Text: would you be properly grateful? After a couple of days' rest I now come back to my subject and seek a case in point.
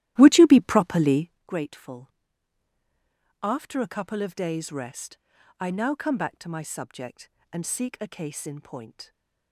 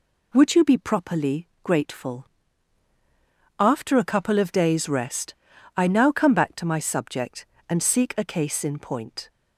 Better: second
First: starts louder than the rest; strong; until 1.4 s; 14 dB // pauses between "properly" and "grateful"; slight; at 1.3 s; 0.18 s long // pauses between "rest" and "I"; at 5.1 s; 0.40 s long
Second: pauses between "properly" and "grateful"; slight; at 1.4 s; 0.18 s long // pauses between "rest" and "I"; at 5.3 s; 0.40 s long

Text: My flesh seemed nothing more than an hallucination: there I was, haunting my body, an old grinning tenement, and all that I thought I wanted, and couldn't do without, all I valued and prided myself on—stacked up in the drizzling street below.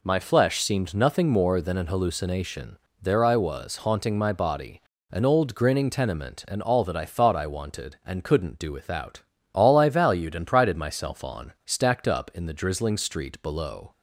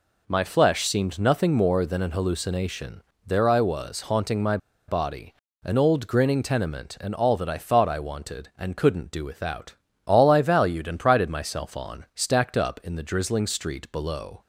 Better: first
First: none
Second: pauses between "my" and "body"; slight; at 4.5 s; 0.31 s long

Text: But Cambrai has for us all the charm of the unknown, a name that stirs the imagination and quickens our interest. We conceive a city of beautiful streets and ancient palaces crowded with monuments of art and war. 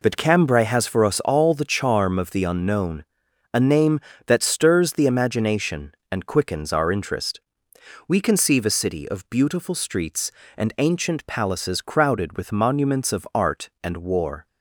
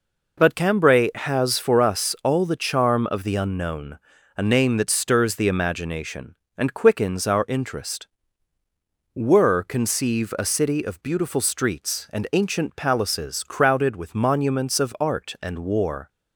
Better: first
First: none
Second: says "Were" for "We"; at 9.1 s

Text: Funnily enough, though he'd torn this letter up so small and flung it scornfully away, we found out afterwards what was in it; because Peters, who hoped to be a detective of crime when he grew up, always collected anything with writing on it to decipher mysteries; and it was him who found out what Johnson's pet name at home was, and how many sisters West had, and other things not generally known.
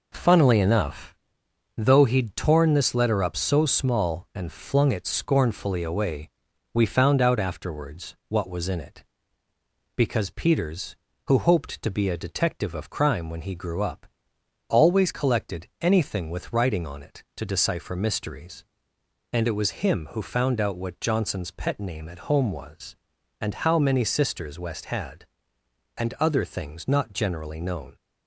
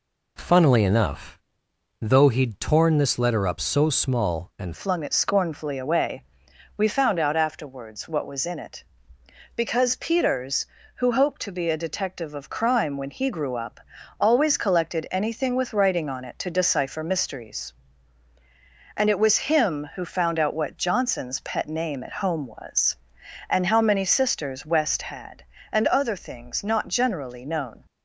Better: first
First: none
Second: changes voice at "flung"; from 4.7 s on; 23.1 s long

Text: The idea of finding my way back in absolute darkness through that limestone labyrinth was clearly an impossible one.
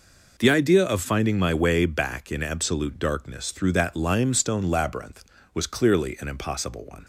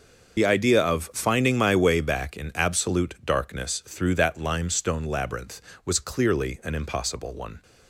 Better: first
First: none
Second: loses the start of "The"; at 0.3 s; 50 ms

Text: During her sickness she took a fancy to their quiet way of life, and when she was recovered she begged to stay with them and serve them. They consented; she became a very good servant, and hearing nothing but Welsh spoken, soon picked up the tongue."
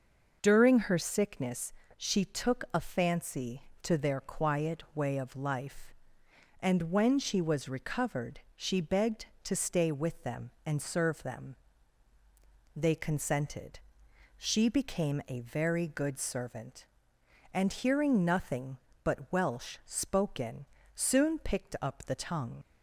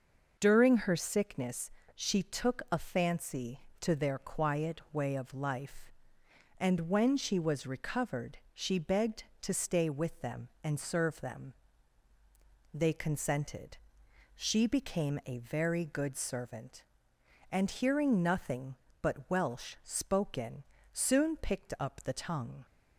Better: second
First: pauses between "sickness" and "she"; slight; at 1.7 s; 0.26 s long // pauses between "recovered" and "she"; slight; at 8.3 s; 0.16 s long // leaves "tongue" unfinished; at 22.6 s; 60 ms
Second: pauses between "sickness" and "she"; slight; at 1.6 s; 0.26 s long // pauses between "recovered" and "she"; slight; at 8.3 s; 0.16 s long

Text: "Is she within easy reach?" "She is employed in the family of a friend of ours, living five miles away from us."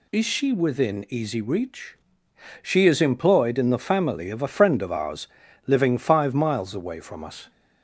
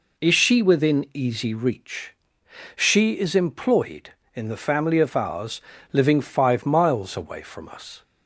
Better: first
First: none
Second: skips "of a friend"; at 4.9 s

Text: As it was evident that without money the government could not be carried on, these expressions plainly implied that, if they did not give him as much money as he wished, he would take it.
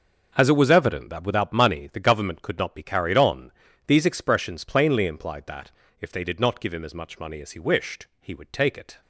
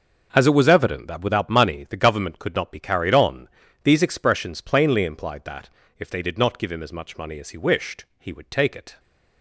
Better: neither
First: starts louder than the rest; noticeable; until 1.3 s; 6 dB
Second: starts louder than the rest; noticeable; until 1.3 s; 6 dB

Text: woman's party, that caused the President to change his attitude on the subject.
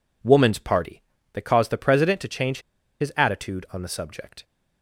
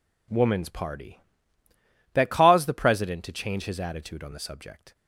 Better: second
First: pauses between "change" and "his"; at 2.5 s; 0.41 s long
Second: none

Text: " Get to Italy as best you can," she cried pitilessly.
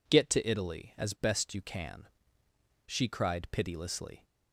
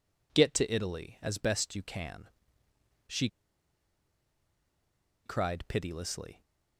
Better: first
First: none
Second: pauses between "she" and "cried"; strong; at 3.2 s; 1.9 s long

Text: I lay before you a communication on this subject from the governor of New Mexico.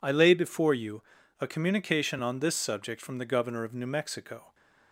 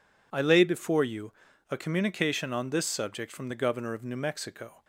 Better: neither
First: pauses between "you" and "a"; at 1.0 s; 0.38 s long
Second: pauses between "you" and "a"; at 1.3 s; 0.38 s long

